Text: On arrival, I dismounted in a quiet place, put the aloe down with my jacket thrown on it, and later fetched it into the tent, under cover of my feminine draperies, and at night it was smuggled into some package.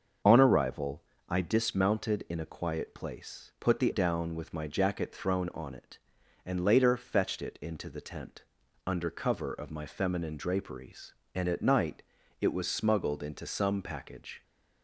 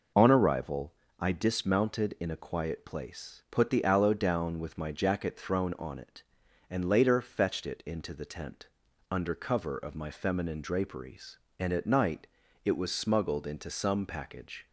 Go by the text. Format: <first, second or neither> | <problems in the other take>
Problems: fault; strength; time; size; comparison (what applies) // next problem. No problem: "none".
second | starts louder than the rest; until 1.5 s; 6.5 dB // skips "aloe"; at 3.9 s // pauses between "night" and "it"; slight; at 12.0 s; 0.36 s long; slight in the second